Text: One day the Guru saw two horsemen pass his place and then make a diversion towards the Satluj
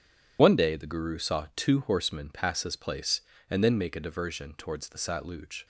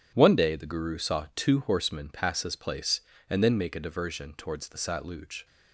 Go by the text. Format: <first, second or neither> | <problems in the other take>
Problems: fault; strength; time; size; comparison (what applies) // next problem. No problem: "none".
second | loses the start of "One"; at 0.3 s; 45 ms